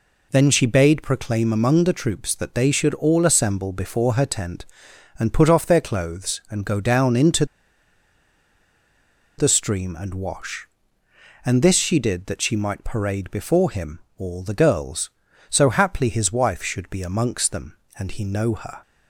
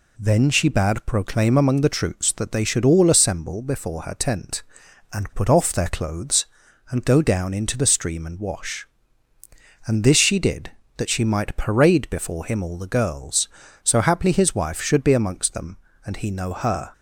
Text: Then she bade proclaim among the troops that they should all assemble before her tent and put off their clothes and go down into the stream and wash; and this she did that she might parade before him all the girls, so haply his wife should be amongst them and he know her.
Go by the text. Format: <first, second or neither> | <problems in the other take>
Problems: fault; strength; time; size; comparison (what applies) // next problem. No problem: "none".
second | pauses between "into" and "the"; strong; at 7.4 s; 1.9 s long // pauses between "him" and "all"; slight; at 13.9 s; 0.18 s long